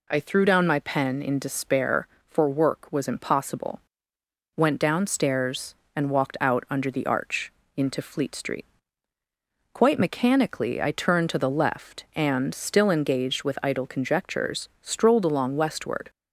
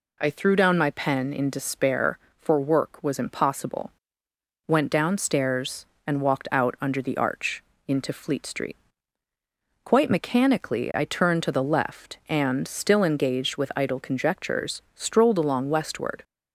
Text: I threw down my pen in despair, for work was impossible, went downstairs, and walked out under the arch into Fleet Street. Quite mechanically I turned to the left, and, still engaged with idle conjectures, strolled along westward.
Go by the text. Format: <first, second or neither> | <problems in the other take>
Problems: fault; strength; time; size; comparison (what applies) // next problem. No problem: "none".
neither | pauses between "arch" and "into"; slight; the same in both